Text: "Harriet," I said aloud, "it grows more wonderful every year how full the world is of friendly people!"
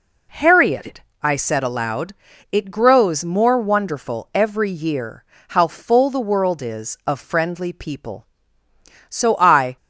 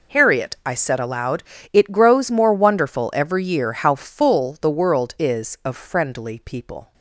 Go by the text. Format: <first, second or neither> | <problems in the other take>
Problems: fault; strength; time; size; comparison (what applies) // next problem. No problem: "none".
second | pauses between "year" and "how"; slight; at 5.2 s; 0.24 s long // goes on to say "So I"; noticeable; from 9.0 s on; 0.68 s long